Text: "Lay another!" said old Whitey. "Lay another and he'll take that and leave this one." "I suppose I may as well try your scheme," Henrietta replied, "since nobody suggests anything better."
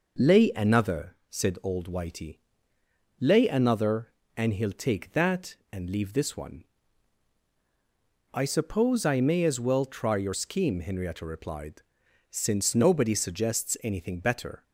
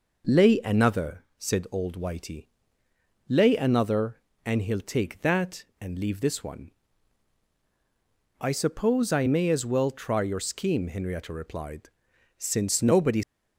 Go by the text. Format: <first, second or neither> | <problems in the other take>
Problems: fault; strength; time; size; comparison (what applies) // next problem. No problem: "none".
first | stops before "suggests anything better"; at 13.2 s